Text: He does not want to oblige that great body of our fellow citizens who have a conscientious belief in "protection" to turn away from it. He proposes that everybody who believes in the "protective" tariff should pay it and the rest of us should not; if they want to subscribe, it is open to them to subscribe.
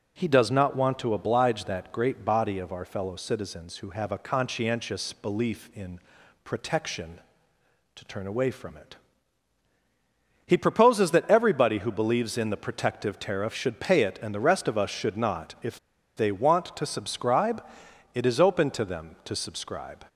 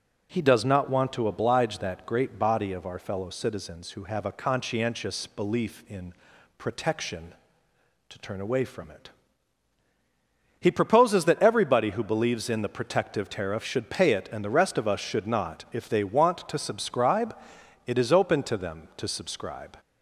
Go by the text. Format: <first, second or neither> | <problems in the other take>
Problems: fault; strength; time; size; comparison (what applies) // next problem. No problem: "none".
second | pauses between "in" and "protection"; at 5.9 s; 0.44 s long; also in the second // pauses between "if" and "they"; at 15.7 s; 0.38 s long